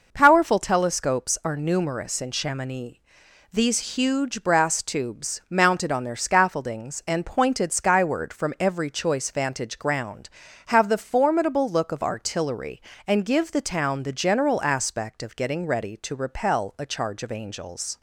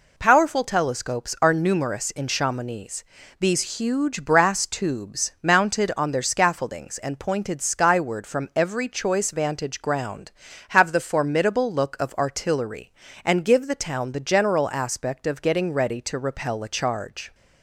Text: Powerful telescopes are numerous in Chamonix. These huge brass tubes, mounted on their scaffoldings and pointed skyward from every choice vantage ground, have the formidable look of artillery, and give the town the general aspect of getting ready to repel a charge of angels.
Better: first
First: none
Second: stops before "of angels"; at 17.3 s

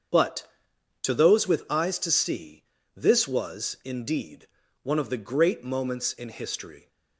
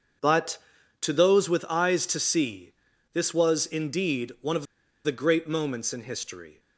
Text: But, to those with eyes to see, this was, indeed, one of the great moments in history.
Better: first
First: starts louder than the rest; until 1.7 s; 7 dB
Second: starts louder than the rest; until 1.6 s; 7 dB // pauses between "of" and "the"; at 4.6 s; 0.39 s long

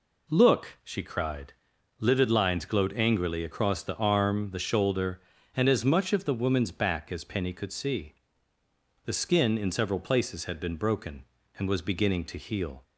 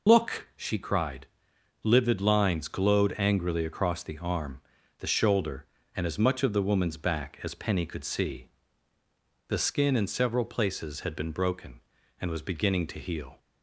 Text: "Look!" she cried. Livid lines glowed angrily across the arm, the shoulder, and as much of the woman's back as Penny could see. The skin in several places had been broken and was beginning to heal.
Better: first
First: none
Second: loses the start of "Look"; at 0.0 s; 25 ms

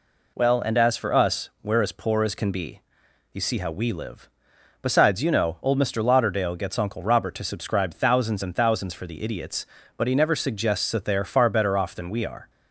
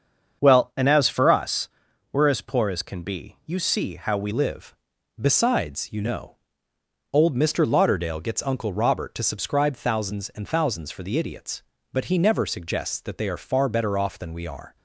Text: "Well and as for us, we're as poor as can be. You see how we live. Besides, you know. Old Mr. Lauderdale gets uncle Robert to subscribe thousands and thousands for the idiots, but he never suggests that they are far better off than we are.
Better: first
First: none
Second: starts louder than the rest; until 1.4 s; 7 dB // changes voice at "live"; from 4.3 s on; 10.4 s long

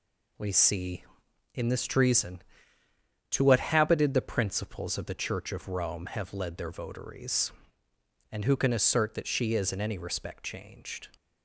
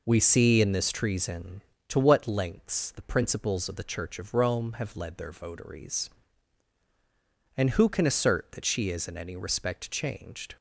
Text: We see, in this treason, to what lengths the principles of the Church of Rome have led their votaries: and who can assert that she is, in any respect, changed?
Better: second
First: says "habited" for "lengths"; at 3.5 s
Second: none

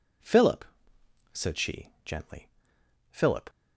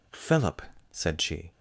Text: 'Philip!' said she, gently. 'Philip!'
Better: first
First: none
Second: stops before "gently Philip"; at 1.5 s

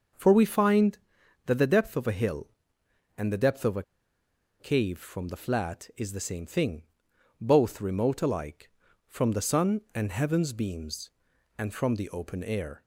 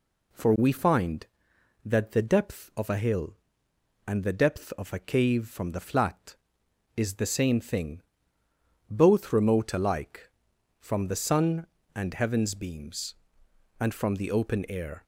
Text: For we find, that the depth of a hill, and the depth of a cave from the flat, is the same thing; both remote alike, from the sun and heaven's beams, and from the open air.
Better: second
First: pauses between "a" and "cave"; noticeable; at 3.8 s; 0.77 s long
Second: none

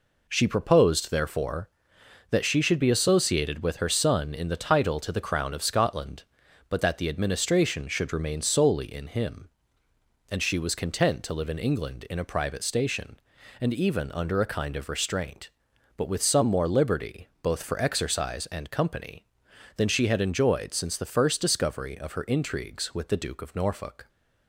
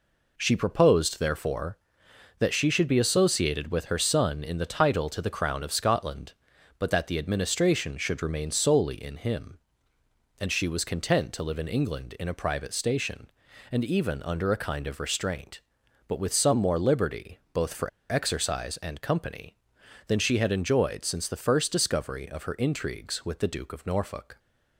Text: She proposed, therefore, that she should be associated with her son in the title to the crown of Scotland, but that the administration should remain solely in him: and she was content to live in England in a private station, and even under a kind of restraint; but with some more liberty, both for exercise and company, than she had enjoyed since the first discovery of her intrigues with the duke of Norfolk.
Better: first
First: none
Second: pauses between "for" and "exercise"; slight; at 17.8 s; 0.21 s long

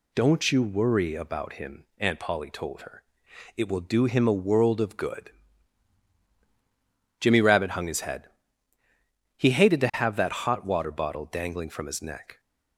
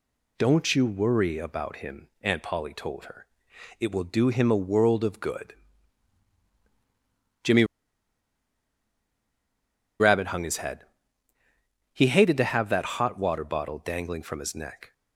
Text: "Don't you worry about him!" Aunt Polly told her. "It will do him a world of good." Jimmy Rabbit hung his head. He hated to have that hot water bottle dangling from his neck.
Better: first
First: none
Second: pauses between "Jimmy" and "Rabbit"; strong; at 7.6 s; 2.3 s long

